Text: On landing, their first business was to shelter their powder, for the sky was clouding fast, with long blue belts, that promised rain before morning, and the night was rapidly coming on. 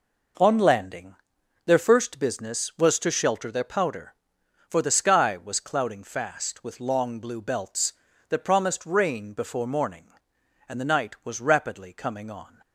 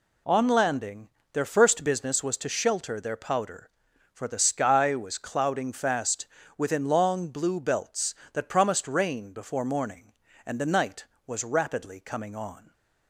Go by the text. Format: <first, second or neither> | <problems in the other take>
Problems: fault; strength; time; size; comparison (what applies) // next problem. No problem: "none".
first | says "within" for "with"; at 6.5 s // stays silent after the last word; slight; from 12.5 s on; 0.5 s long